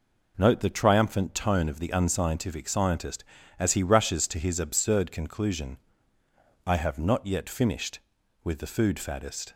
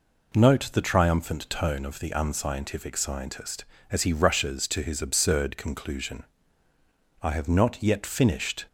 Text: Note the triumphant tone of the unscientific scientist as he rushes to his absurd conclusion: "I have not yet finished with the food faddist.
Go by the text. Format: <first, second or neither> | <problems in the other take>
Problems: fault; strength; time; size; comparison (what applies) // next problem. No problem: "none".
first | stops before "with the food faddist"; at 8.6 s